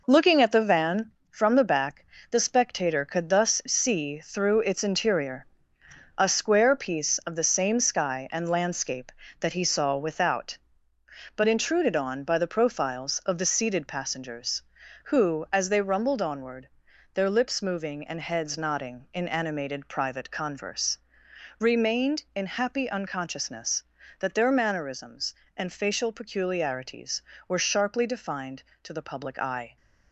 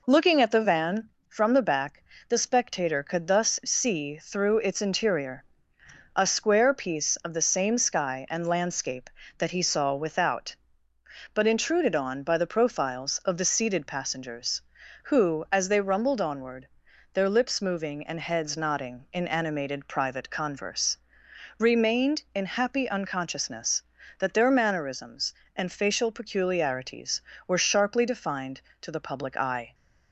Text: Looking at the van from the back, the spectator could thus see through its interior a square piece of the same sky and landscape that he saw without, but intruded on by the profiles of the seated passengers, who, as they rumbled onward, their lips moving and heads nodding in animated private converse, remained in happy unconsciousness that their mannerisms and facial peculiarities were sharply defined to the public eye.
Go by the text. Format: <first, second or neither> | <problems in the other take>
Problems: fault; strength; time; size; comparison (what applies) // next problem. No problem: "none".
second | gets quieter; throughout; 7 dB // pauses between "interior" and "a"; noticeable; at 5.4 s; 0.72 s long; noticeable in the second